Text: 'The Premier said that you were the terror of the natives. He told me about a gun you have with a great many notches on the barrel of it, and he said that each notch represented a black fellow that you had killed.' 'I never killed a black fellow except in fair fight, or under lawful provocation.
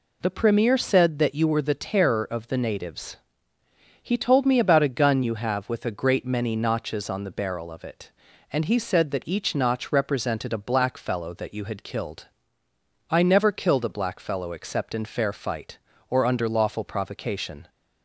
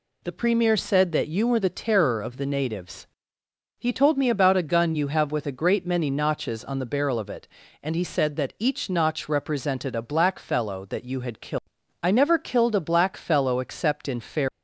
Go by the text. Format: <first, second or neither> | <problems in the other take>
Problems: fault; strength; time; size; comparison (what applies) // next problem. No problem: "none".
first | stops before "fight or under lawful provocation"; at 14.4 s